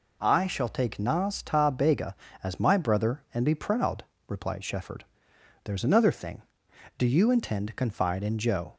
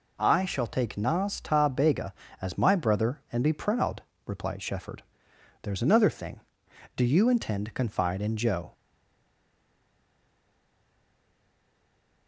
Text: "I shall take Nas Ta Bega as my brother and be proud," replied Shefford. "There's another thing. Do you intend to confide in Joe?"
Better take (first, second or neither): first